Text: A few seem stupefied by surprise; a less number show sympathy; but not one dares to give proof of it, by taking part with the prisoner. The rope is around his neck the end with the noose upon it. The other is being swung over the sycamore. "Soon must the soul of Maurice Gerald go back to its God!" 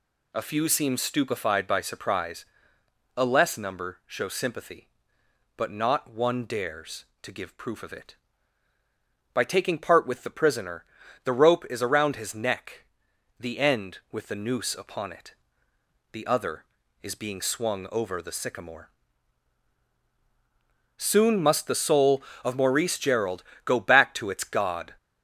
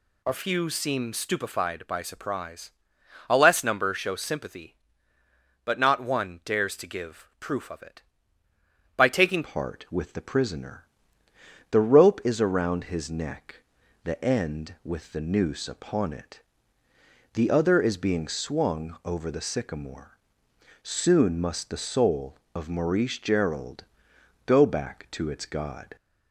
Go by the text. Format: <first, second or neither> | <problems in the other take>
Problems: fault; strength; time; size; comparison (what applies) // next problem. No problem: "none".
first | changes voice at "part"; from 9.4 s on; 16.5 s long // pauses between "neck" and "the"; noticeable; at 13.5 s; 0.46 s long; noticeable in the first // pauses between "Gerald" and "go"; noticeable; at 23.8 s; 0.62 s long; slight in the first